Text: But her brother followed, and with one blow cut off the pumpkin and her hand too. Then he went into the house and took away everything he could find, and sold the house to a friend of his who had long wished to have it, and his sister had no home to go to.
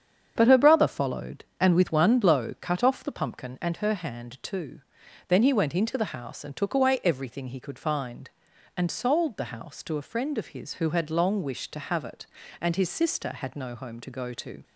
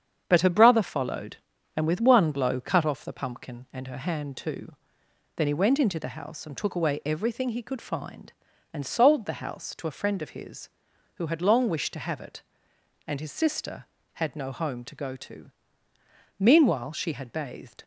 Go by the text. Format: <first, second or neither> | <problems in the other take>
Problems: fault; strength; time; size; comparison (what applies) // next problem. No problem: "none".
first | starts louder than the rest; strong; until 1.2 s; 8 dB; strong in the first // goes on to say "Meanwhile she had bathed"; from 16.3 s on; 1.4 s long